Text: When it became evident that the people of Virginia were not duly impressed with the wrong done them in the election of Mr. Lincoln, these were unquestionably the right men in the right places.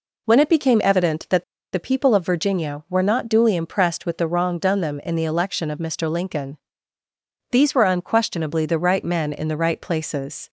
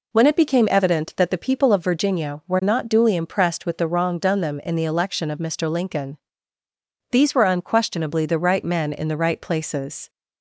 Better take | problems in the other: second | pauses between "that" and "the"; slight; at 1.4 s; 0.30 s long

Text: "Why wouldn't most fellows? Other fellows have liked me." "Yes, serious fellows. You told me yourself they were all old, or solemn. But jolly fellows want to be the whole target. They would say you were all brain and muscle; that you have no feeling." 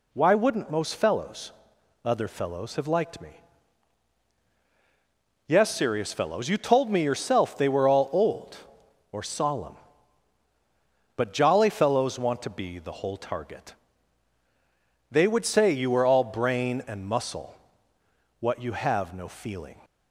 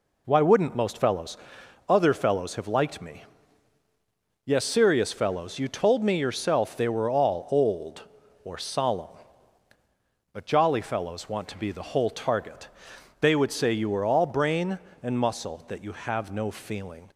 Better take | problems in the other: second | says "what" for "that"; at 18.3 s

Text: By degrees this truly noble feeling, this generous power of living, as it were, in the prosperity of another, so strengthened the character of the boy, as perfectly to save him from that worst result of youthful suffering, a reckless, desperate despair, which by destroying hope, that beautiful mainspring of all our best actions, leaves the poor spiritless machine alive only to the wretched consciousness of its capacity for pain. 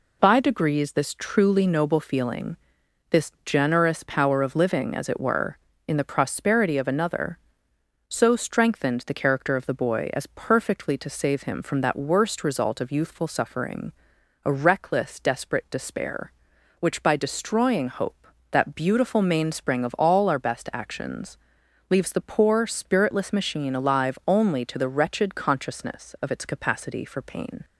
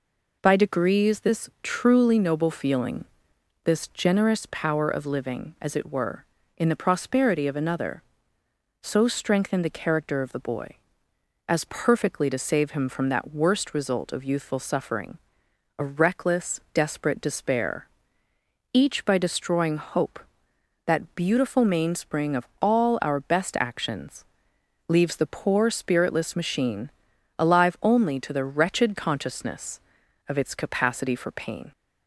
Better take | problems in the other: first | says "each" for "which"; at 18.7 s // pauses between "of" and "all"; slight; at 22.4 s; 0.16 s long // pauses between "machine" and "alive"; noticeable; at 26.9 s; 0.48 s long

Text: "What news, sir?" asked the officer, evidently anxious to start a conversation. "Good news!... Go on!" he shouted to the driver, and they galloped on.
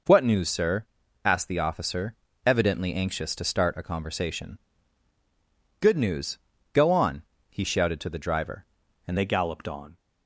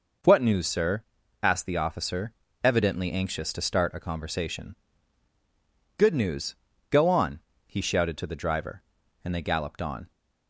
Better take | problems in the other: second | changes voice at "they"; from 9.1 s on; 0.8 s long

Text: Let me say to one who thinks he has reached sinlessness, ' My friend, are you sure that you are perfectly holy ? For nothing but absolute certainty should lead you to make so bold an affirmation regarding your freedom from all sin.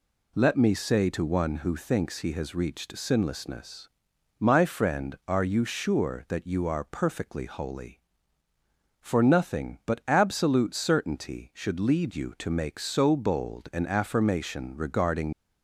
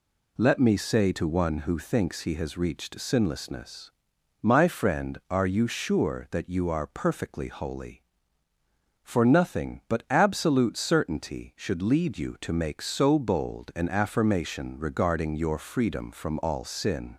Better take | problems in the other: second | stops before "your freedom from all sin"; at 15.3 s

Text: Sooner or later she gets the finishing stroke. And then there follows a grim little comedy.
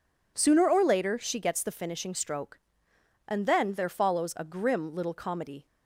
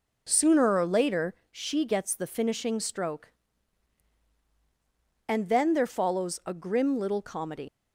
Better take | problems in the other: first | pauses between "later" and "she"; slight; at 1.3 s; 0.18 s long // leaves "comedy" unfinished; at 7.6 s; 90 ms

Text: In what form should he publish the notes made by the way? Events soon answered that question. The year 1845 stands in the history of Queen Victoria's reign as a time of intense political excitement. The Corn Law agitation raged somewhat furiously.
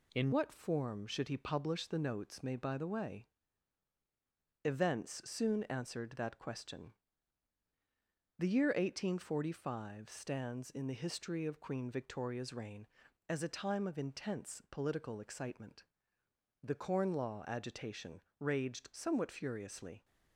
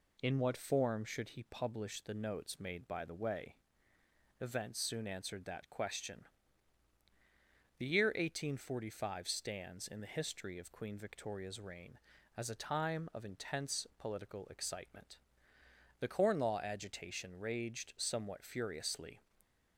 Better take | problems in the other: second | changes voice at "what"; from 0.3 s on; 19.7 s long // pauses between "agitation" and "raged"; slight; at 18.2 s; 0.16 s long

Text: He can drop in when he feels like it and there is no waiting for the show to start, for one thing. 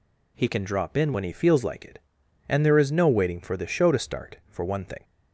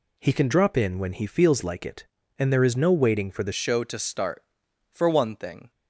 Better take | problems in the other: first | changes voice at "show"; from 3.5 s on; 2.2 s long

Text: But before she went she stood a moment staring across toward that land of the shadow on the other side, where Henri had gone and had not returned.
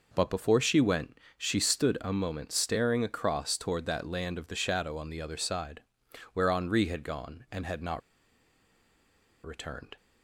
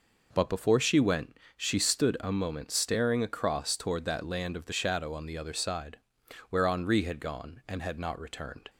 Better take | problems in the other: second | pauses between "went" and "she"; slight; at 1.1 s; 0.20 s long; slight in the second // pauses between "not" and "returned"; strong; at 8.0 s; 1.4 s long

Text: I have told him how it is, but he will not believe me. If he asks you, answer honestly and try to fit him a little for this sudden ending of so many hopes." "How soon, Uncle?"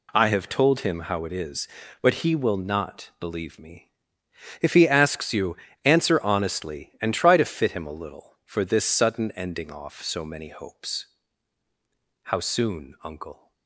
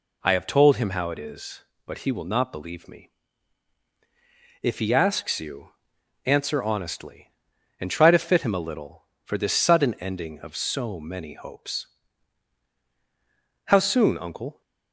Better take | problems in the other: second | says "off" for "of"; at 9.7 s

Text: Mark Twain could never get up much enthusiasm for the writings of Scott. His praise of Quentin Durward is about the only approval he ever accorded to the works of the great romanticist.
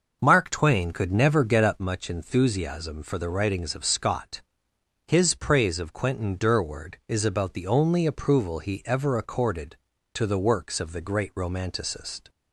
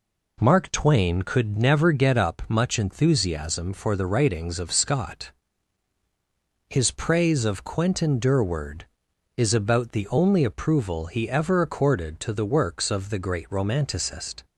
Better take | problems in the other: second | starts louder than the rest; noticeable; until 1.9 s; 6 dB

